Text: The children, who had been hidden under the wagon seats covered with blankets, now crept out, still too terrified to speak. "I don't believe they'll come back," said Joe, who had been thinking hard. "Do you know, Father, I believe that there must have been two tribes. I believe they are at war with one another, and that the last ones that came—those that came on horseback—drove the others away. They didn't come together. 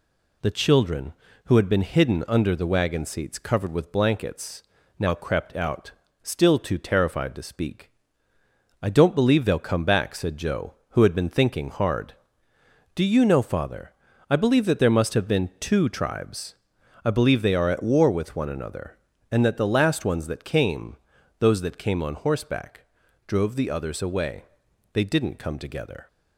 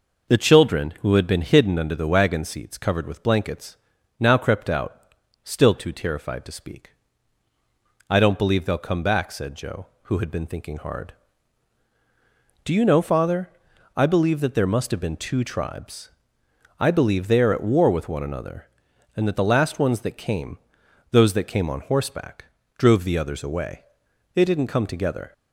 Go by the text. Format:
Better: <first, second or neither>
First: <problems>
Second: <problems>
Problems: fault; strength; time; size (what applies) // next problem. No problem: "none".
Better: neither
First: none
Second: none